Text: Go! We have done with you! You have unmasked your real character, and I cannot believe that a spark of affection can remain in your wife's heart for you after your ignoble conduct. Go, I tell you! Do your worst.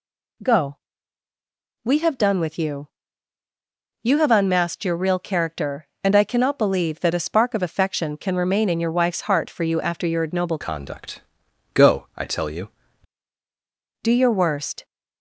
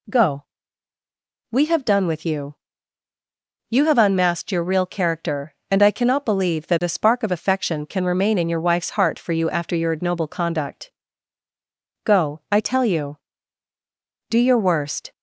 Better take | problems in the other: second | changes voice from "conduct" to "you"; from 10.6 to 12.6 s; 2.0 s long

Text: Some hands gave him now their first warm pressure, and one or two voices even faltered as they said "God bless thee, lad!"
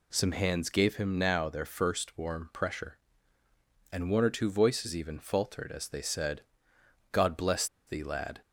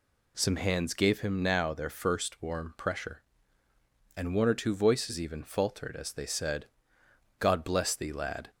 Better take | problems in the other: second | pauses between "said" and "God"; noticeable; at 6.4 s; 0.72 s long; noticeable in the second // pauses between "bless" and "thee"; slight; at 7.6 s; 0.21 s long

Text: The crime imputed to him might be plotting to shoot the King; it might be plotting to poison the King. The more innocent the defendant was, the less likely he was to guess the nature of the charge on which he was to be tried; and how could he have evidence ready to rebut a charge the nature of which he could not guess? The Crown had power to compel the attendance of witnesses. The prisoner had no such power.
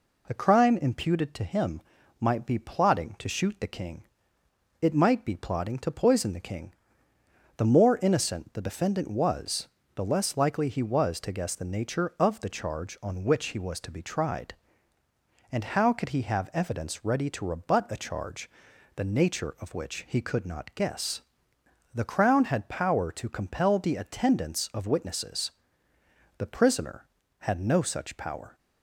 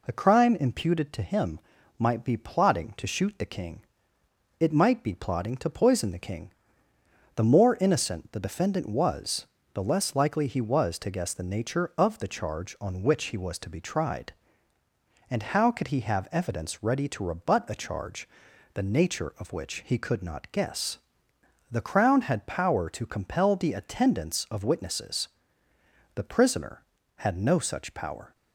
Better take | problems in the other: neither | pauses between "him" and "might"; the same in both // pauses between "charge" and "the"; noticeable; the same in both

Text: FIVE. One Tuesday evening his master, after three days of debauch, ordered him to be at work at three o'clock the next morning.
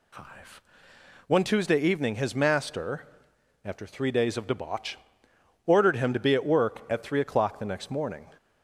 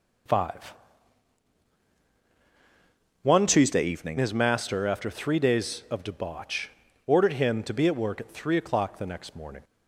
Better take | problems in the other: first | changes voice from "Tuesday" to "evening"; from 3.4 to 4.1 s; 0.7 s long

